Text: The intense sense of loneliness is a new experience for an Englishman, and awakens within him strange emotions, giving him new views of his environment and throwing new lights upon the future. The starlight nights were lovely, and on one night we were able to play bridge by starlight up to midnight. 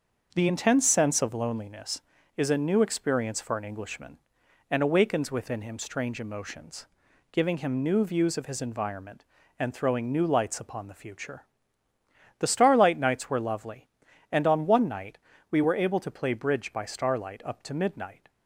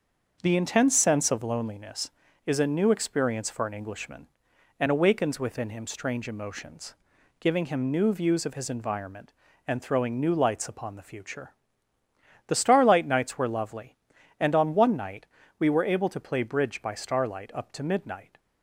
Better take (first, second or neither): neither